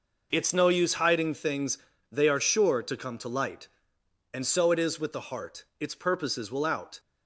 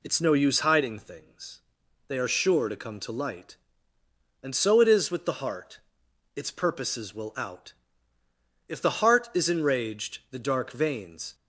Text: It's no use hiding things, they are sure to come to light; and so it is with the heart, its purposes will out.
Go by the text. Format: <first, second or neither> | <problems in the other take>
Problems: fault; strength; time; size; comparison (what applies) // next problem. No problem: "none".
first | goes on to say "If the heart is enraged the dark veins"; strong; from 8.6 s on; 2.6 s long